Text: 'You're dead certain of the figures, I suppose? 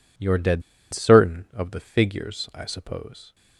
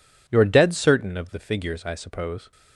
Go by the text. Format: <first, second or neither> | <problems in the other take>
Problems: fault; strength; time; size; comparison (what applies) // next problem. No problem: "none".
second | pauses between "dead" and "certain"; slight; at 0.6 s; 0.30 s long